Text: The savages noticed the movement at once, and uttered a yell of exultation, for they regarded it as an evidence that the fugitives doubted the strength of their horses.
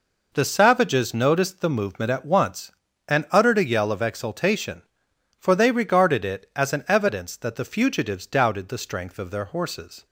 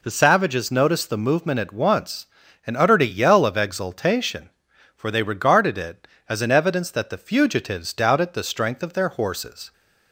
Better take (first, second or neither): neither